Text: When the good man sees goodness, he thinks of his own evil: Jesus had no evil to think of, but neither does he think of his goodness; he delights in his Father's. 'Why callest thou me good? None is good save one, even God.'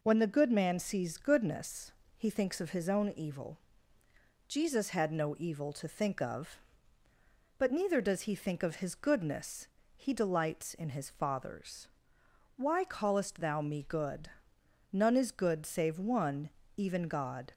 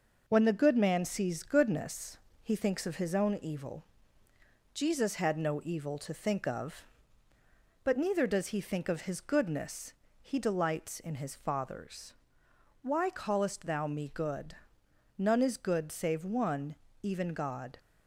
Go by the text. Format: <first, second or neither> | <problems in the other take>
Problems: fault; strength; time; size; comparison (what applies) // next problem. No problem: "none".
first | gets quieter; throughout; 3.5 dB